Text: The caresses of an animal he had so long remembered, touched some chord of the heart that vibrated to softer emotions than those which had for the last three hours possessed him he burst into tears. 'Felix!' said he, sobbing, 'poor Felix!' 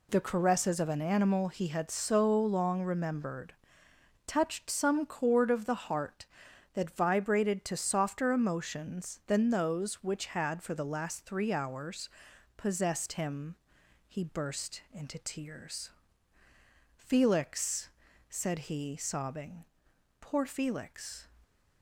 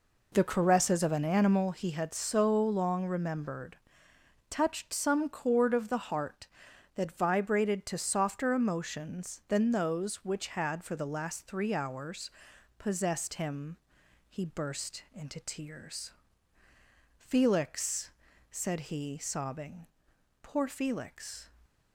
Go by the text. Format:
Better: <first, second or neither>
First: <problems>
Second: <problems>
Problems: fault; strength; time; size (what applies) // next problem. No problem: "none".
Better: first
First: pauses between "hours" and "possessed"; noticeable; at 12.0 s; 0.48 s long // pauses between "him" and "he"; noticeable; at 13.5 s; 0.52 s long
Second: starts louder than the rest; until 1.7 s; 4 dB // pauses between "hours" and "possessed"; noticeable; at 12.2 s; 0.48 s long // pauses between "him" and "he"; noticeable; at 13.7 s; 0.52 s long